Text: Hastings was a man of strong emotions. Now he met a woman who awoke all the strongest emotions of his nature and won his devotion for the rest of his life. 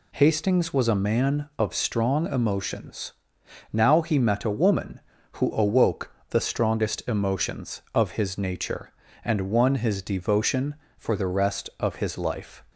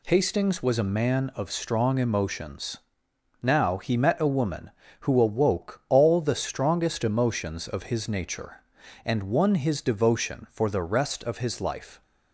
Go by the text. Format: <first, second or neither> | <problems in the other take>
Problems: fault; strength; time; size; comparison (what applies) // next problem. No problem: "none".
second | skips "all"; at 6.2 s